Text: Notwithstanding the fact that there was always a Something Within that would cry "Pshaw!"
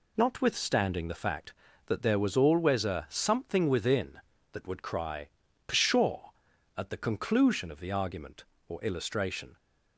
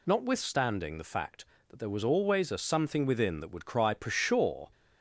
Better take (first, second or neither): second